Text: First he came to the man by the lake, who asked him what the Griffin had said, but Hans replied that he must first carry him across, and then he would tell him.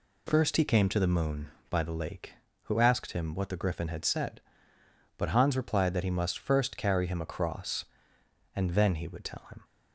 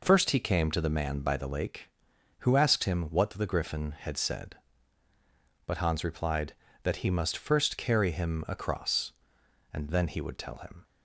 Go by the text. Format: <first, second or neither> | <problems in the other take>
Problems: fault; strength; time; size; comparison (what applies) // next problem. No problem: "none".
second | says "moon" for "man"; at 1.0 s